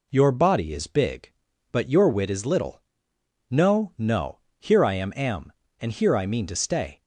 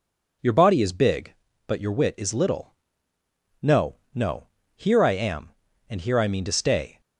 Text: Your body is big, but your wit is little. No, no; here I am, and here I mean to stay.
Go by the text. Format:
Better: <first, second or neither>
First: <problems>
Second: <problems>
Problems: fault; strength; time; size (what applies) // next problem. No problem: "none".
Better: second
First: says "am" twice; at 5.1 s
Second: none